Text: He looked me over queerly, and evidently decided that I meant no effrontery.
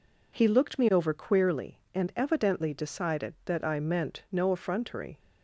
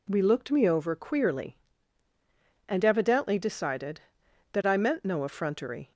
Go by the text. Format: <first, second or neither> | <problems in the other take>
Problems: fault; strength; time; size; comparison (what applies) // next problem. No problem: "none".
first | says "We" for "He"; at 0.0 s